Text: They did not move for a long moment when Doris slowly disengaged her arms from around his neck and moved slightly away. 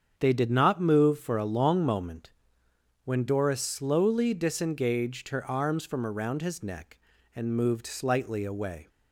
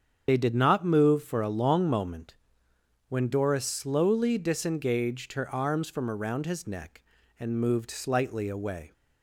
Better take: first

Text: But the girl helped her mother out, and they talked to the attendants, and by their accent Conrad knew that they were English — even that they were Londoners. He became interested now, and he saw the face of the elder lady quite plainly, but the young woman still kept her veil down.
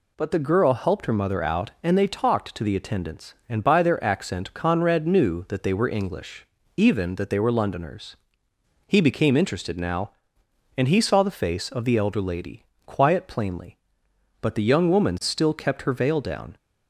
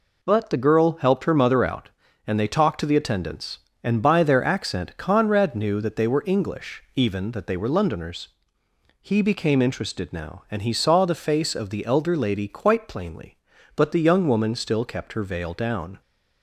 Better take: second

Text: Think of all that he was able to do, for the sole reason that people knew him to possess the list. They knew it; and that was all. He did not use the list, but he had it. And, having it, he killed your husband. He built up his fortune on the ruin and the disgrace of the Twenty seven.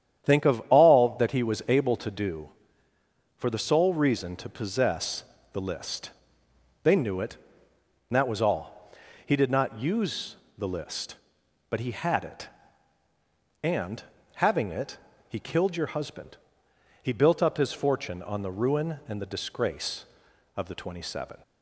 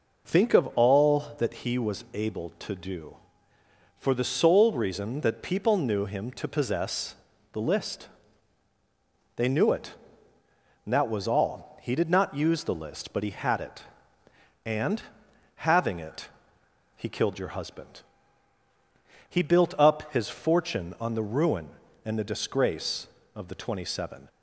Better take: second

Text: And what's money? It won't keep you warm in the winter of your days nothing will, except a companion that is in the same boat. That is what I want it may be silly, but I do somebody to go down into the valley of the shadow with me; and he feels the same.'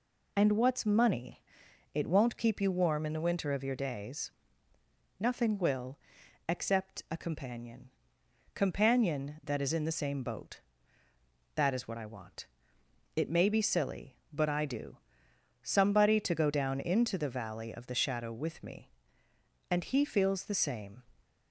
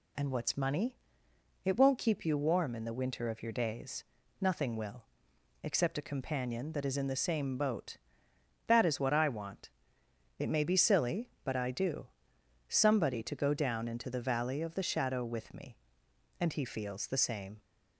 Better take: second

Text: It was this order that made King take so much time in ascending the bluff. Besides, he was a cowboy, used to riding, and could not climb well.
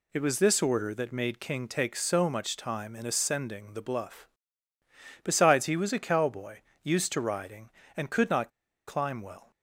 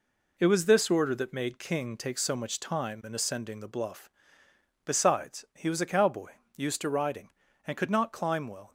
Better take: second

